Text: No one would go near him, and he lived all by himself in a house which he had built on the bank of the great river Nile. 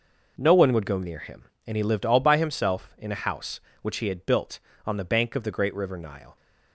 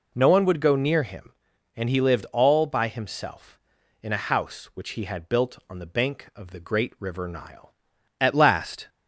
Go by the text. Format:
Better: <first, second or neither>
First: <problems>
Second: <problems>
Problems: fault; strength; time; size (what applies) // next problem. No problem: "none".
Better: first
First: none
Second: goes on to say "At last"; noticeable; from 8.2 s on; 0.68 s long